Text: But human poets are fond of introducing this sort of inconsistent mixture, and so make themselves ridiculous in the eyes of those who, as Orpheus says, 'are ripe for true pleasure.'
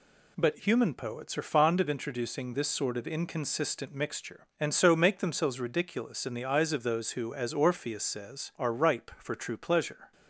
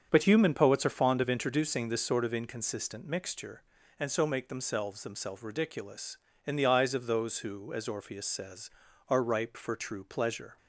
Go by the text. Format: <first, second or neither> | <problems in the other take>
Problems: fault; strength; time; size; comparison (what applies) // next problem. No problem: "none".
first | starts louder than the rest; strong; until 1.1 s; 7 dB // says "themselves" twice; at 5.0 s